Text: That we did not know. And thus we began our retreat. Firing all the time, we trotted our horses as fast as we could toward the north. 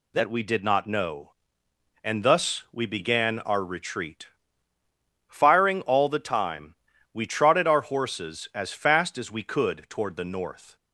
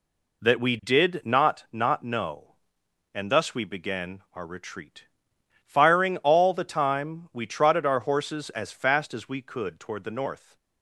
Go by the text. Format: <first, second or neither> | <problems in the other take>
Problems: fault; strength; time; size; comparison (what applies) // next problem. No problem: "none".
first | says "not" twice; at 1.7 s